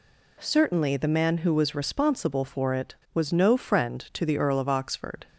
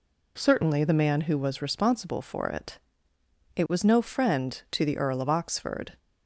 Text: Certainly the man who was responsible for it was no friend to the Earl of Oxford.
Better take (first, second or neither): first